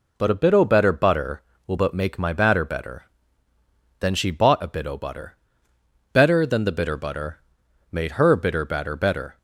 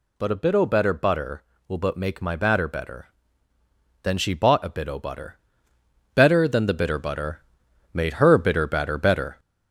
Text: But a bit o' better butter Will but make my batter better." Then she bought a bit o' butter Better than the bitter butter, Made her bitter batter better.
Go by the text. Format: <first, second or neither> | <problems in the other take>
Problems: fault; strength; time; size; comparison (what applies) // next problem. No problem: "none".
first | gets louder; slight; throughout; 3 dB // pauses between "butter" and "Better"; noticeable; at 5.3 s; 0.74 s long; noticeable in the first